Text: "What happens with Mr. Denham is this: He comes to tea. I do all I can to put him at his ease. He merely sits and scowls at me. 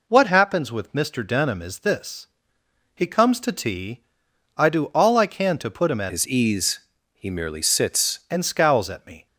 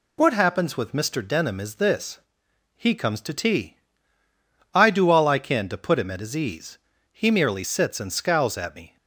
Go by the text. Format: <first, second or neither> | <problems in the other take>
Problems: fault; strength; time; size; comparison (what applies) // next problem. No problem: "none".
second | changes voice from "his" to "sits"; from 6.1 to 8.1 s; 2.0 s long